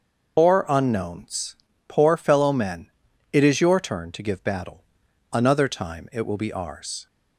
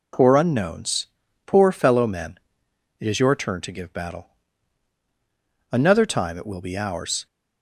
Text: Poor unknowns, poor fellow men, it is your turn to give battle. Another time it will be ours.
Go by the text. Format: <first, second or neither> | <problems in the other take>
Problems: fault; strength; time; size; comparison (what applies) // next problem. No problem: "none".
second | loses the start of "Poor"; at 0.3 s; 110 ms